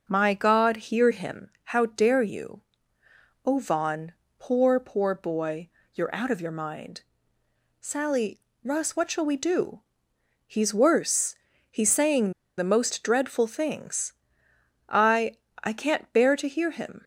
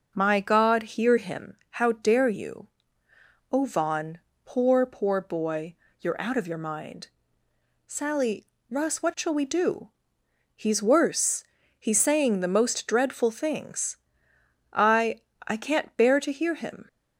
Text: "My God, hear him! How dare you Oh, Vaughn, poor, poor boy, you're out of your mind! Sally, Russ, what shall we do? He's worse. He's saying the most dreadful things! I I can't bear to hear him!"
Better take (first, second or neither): second